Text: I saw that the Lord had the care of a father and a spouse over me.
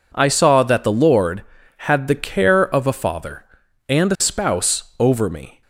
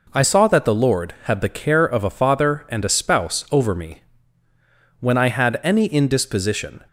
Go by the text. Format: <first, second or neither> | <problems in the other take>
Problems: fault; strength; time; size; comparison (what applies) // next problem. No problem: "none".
first | goes on to say "When I had any indisposition"; strong; from 5.0 s on; 1.8 s long